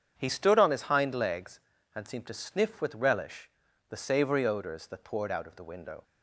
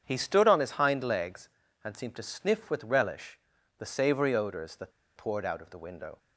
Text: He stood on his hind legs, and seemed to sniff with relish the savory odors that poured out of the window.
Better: first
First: starts louder than the rest; strong; until 1.1 s; 8 dB // pauses between "relish" and "the"; at 3.4 s; 0.40 s long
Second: starts louder than the rest; strong; until 1.0 s; 8 dB // pauses between "relish" and "the"; at 3.3 s; 0.40 s long // pauses between "that" and "poured"; slight; at 4.9 s; 0.25 s long

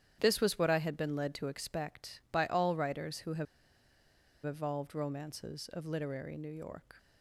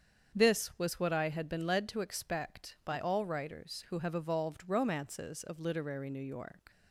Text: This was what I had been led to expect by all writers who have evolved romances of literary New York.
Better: second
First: starts louder than the rest; strong; until 1.2 s; 10 dB // pauses between "have" and "evolved"; at 3.4 s; 1.0 s long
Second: starts louder than the rest; strong; until 1.4 s; 7.5 dB

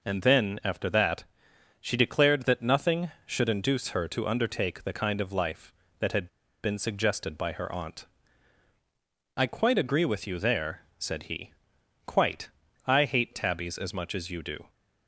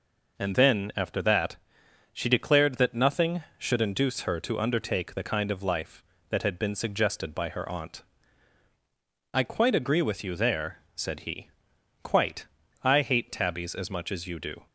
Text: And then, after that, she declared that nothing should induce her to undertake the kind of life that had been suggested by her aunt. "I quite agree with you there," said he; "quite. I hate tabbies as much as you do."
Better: second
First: pauses between "had" and "been"; slight; at 6.2 s; 0.35 s long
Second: none

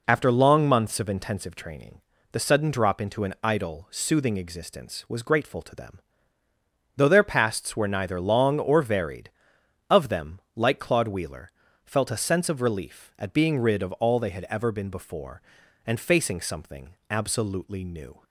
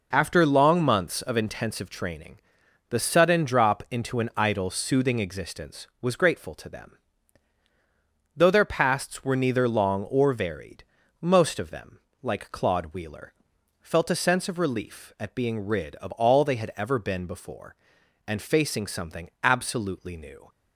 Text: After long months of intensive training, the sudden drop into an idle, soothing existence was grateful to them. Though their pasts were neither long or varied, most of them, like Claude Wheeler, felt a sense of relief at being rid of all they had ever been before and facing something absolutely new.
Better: second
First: skips "most"; at 9.5 s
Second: none

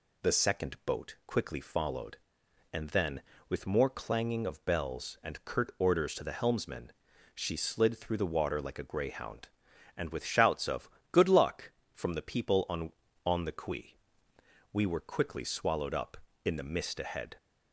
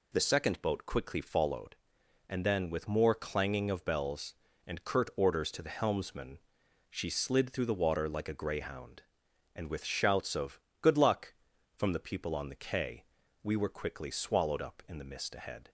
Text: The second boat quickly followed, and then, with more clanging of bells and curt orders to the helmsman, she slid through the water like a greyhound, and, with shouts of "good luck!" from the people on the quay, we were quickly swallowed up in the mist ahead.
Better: second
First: pauses between "of" and "good"; slight; at 10.8 s; 0.22 s long // says "on" twice; at 13.2 s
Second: pauses between "of" and "good"; slight; at 10.5 s; 0.24 s long

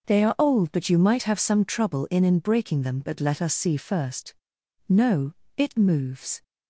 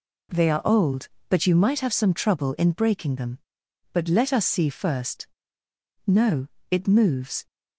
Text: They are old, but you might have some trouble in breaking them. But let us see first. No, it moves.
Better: second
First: says "in" twice; at 2.2 s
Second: none

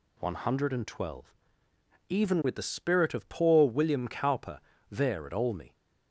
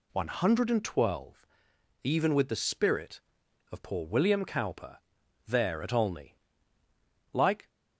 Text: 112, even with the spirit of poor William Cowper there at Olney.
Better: first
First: pauses between "Cowper" and "there"; slight; at 4.5 s; 0.32 s long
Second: pauses between "Cowper" and "there"; noticeable; at 5.0 s; 0.46 s long // goes on to say "Like"; slight; from 7.3 s on; 0.34 s long

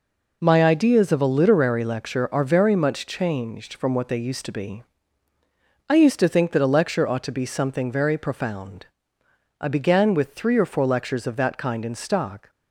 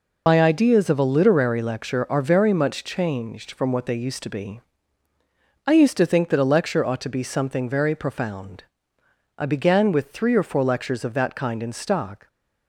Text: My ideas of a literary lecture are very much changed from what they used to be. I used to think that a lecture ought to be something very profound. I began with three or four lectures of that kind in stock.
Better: first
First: none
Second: loses the start of "My"; at 0.2 s; 70 ms

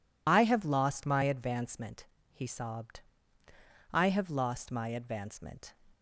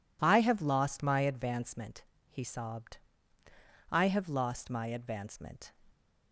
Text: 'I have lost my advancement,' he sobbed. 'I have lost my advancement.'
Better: second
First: loses the start of "I"; at 0.2 s; 45 ms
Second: none

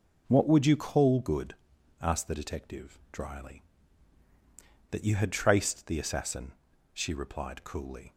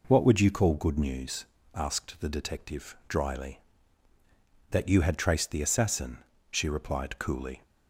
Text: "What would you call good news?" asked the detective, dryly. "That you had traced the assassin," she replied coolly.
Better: second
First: skips "news"; at 1.7 s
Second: none

